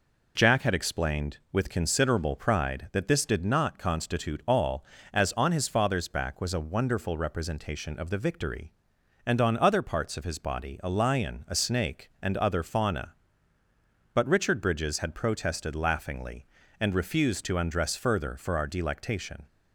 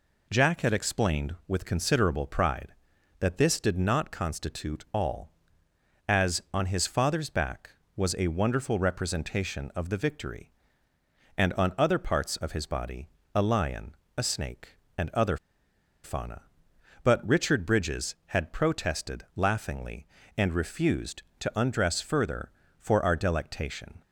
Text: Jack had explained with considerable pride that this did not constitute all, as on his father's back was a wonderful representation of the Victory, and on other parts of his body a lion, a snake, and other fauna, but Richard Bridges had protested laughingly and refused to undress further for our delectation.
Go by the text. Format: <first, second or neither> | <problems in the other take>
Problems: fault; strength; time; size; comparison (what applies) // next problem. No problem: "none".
first | pauses between "body" and "a"; slight; at 13.0 s; 0.26 s long // pauses between "other" and "fauna"; noticeable; at 15.3 s; 0.67 s long